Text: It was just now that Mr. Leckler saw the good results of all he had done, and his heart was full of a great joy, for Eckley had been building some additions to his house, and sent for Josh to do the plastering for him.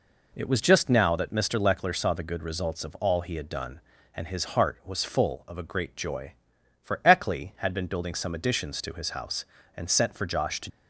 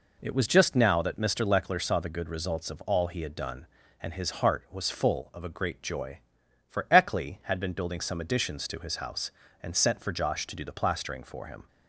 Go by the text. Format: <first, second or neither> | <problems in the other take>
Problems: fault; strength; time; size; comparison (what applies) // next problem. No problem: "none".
second | stops before "do the plastering for him"; at 10.6 s